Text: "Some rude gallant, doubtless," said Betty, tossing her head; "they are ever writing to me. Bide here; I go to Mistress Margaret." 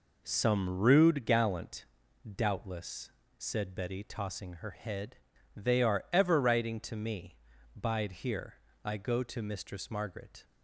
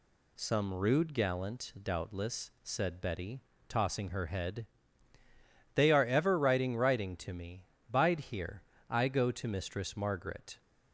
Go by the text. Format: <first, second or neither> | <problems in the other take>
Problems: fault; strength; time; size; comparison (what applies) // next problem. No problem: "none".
first | says "writing" twice; at 6.7 s